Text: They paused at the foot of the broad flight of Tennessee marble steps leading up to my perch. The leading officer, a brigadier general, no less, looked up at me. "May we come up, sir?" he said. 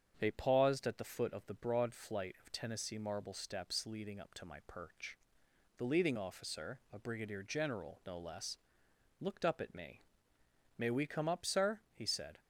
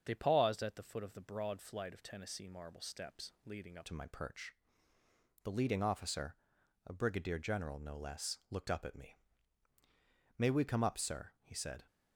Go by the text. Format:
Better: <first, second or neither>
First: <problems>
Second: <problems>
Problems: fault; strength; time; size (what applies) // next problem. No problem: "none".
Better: first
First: starts louder than the rest; strong; until 1.2 s; 7.5 dB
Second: starts louder than the rest; until 1.0 s; 6.5 dB // changes voice at "to"; from 3.8 s on; 8.0 s long